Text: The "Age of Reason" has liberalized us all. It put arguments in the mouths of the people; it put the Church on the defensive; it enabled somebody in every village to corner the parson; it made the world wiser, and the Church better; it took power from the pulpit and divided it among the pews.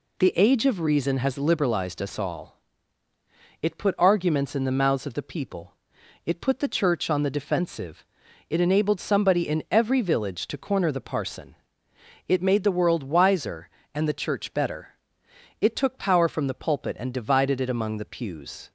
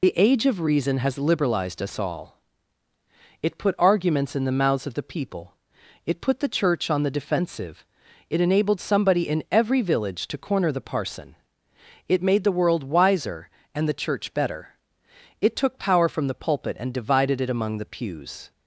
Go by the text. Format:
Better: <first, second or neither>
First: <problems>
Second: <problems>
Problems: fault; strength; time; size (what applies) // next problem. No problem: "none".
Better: first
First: none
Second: loses the start of "The"; at 0.0 s; 35 ms